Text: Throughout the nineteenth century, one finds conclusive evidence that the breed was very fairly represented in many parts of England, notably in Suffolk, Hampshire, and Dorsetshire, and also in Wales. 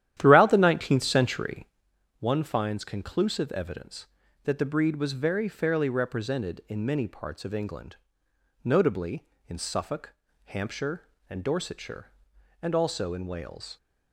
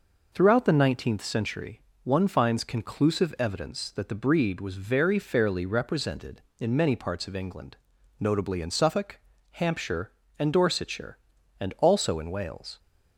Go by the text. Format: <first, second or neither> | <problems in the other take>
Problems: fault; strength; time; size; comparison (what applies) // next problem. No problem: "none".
second | starts louder than the rest; strong; until 1.9 s; 11.5 dB